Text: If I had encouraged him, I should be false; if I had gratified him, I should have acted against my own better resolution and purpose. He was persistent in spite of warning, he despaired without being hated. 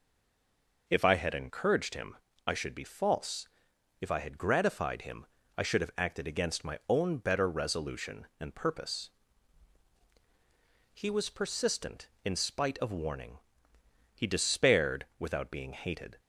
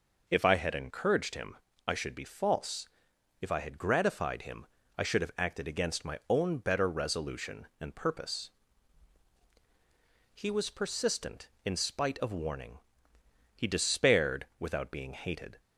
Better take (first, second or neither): second